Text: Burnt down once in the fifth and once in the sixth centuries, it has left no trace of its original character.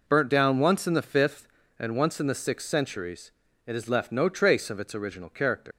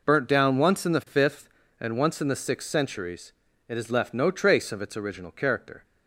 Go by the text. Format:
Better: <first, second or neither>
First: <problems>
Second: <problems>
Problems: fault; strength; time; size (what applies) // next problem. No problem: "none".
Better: second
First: leaves "character" unfinished; at 5.7 s; 105 ms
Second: none